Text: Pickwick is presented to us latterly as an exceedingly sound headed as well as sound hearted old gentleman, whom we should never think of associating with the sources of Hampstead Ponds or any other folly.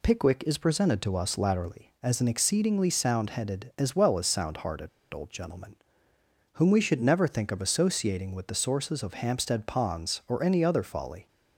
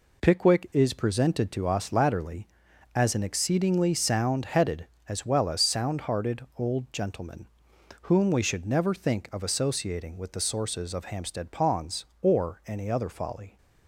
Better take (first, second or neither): second